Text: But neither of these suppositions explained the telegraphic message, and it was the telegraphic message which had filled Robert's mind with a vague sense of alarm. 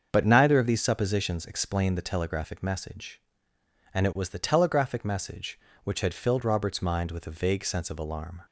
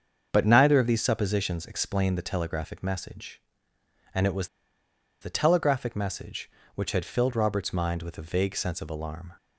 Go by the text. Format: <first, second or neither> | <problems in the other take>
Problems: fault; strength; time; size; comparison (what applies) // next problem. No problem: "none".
first | starts louder than the rest; until 1.3 s; 7 dB; also in the first // pauses between "was" and "the"; noticeable; at 4.4 s; 0.74 s long